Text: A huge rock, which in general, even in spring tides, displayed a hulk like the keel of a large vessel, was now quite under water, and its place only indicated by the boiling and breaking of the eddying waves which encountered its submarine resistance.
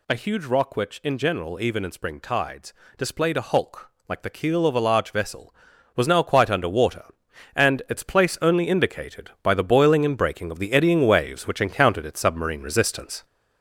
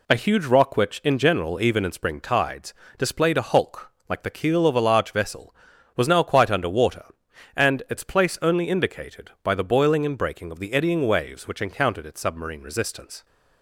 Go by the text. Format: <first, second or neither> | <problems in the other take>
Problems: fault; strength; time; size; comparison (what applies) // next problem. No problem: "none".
second | gets louder; noticeable; throughout; 5.5 dB // pauses between "hulk" and "like"; slight; at 3.9 s; 0.16 s long; slight in the second